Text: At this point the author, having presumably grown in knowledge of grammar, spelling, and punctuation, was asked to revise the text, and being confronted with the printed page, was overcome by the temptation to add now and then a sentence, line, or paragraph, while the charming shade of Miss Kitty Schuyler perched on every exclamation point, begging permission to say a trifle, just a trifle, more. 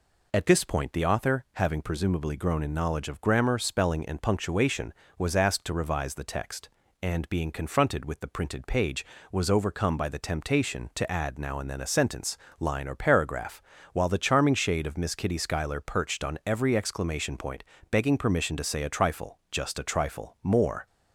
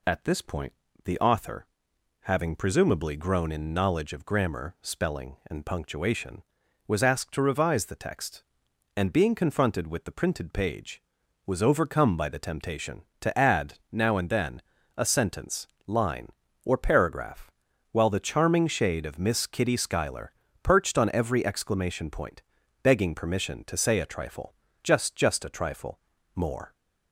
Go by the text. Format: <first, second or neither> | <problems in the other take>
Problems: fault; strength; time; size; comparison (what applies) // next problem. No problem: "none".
first | pauses between "point" and "the"; slight; at 0.7 s; 0.32 s long // pauses between "add" and "now"; slight; at 13.7 s; 0.18 s long // pauses between "then" and "a"; slight; at 14.6 s; 0.34 s long // pauses between "Schuyler" and "perched"; slight; at 20.3 s; 0.32 s long // says "just" twice; at 25.1 s